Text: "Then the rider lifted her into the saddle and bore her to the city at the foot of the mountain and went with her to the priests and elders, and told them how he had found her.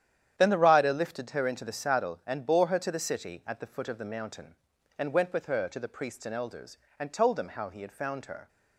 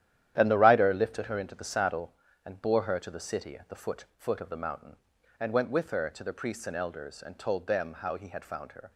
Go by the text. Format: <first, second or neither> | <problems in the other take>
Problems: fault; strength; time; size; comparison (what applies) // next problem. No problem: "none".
first | starts louder than the rest; strong; until 1.3 s; 11 dB; strong in the first // says "foot" twice; at 4.1 s